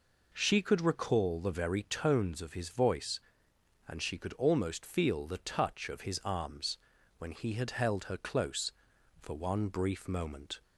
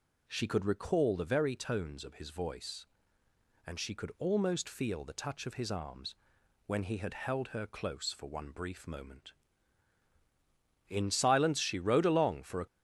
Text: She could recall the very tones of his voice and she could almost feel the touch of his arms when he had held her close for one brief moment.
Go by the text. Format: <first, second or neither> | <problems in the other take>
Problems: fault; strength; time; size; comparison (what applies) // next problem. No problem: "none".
first | pauses between "arms" and "when"; noticeable; at 6.1 s; 0.52 s long; also in the first // goes on to say "In silence she rode along for a"; strong; from 10.8 s on; 1.7 s long